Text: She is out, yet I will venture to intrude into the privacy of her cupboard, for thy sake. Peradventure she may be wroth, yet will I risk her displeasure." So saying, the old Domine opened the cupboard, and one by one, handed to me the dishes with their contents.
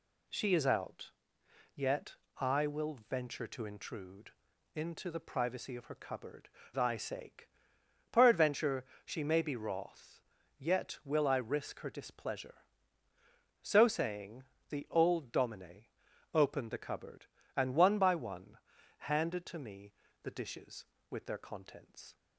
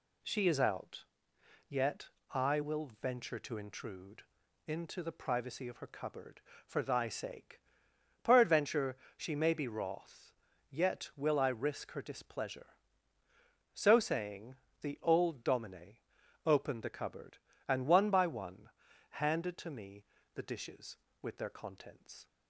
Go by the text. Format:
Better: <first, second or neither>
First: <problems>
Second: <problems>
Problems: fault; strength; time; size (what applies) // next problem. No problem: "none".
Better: second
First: pauses between "yet" and "I"; slight; at 2.1 s; 0.24 s long // pauses between "intrude" and "into"; at 4.3 s; 0.44 s long // skips "for"; at 6.6 s // pauses between "Peradventure" and "she"; slight; at 8.8 s; 0.20 s long // pauses between "Domine" and "opened"; noticeable; at 15.8 s; 0.48 s long // pauses between "me" and "the"; slight; at 19.9 s; 0.32 s long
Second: pauses between "yet" and "I"; slight; at 2.0 s; 0.24 s long // pauses between "intrude" and "into"; at 4.2 s; 0.44 s long // pauses between "Peradventure" and "she"; slight; at 8.9 s; 0.20 s long // pauses between "Domine" and "opened"; noticeable; at 15.9 s; 0.48 s long // pauses between "me" and "the"; slight; at 20.0 s; 0.32 s long